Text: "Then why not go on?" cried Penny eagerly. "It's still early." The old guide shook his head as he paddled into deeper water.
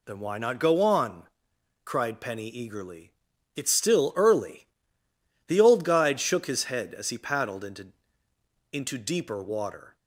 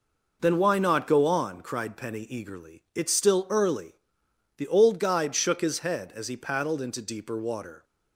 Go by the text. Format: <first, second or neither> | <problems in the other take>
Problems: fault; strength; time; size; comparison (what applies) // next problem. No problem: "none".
second | says "into" twice; at 8.7 s